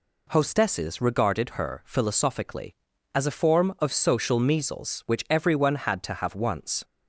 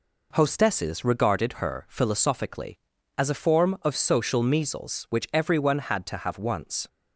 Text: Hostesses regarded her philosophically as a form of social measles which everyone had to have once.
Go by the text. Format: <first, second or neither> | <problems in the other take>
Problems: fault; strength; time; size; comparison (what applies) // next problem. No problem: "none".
first | gets quieter; throughout; 3.5 dB